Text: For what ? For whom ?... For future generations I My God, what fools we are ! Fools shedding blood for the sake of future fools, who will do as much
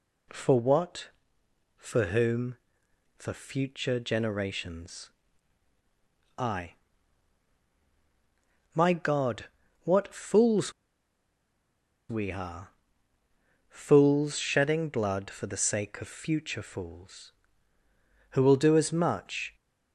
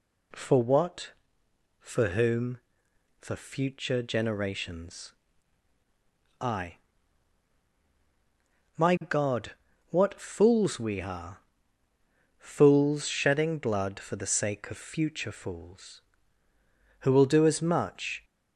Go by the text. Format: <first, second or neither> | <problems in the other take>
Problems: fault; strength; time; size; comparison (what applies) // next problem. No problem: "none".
second | pauses between "generations" and "I"; strong; at 5.0 s; 1.2 s long; strong in the second // pauses between "I" and "My"; strong; at 6.7 s; 2.0 s long; strong in the second // pauses between "fools" and "we"; strong; at 10.7 s; 1.3 s long